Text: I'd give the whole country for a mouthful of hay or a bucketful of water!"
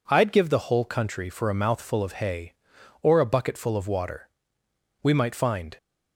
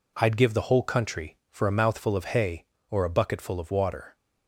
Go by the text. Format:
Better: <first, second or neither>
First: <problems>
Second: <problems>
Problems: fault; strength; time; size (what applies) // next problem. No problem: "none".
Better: second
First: goes on to say "We might find"; noticeable; from 5.0 s on; 0.76 s long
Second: none